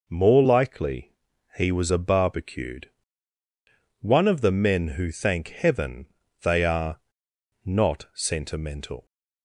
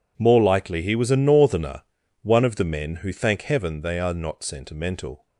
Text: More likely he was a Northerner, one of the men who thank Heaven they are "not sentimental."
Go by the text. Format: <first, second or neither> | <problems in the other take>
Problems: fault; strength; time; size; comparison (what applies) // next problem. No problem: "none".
second | pauses between "likely" and "he"; at 1.1 s; 0.42 s long // says "Barbecued" for "Northerner"; at 1.9 s // pauses between "Heaven" and "they"; slight; at 6.0 s; 0.36 s long // pauses between "are" and "not"; noticeable; at 6.9 s; 0.64 s long